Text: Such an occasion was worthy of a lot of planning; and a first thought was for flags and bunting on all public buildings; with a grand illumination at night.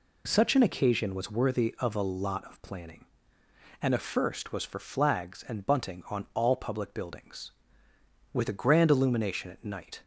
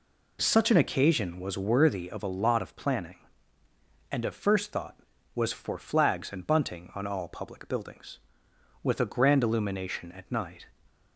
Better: second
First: skips "thought"; at 4.5 s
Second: none

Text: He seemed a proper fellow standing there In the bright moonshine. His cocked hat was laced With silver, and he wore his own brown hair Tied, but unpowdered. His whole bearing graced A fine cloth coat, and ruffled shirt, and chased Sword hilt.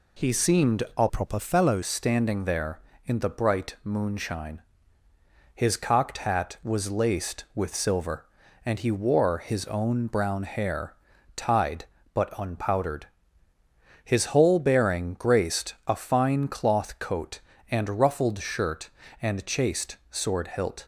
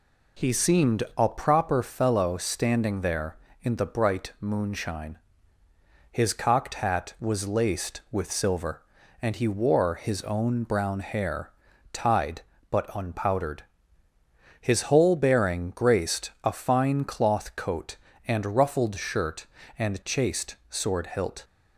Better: second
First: pauses between "seemed" and "a"; slight; at 0.8 s; 0.16 s long // changes voice from "proper" to "fellow"; from 1.0 to 1.8 s; 0.8 s long // pauses between "hair" and "Tied"; at 10.9 s; 0.42 s long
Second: pauses between "seemed" and "a"; slight; at 1.0 s; 0.16 s long // pauses between "hair" and "Tied"; at 11.4 s; 0.42 s long

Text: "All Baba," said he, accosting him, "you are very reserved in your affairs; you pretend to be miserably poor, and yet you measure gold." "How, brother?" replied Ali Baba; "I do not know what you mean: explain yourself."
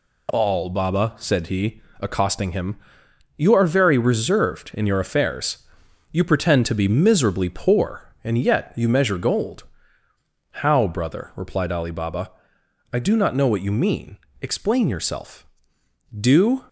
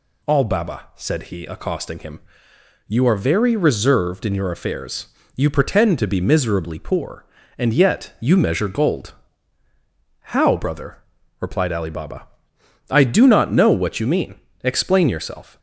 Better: second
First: goes on to say "Do"; slight; from 16.1 s on; 0.48 s long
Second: none

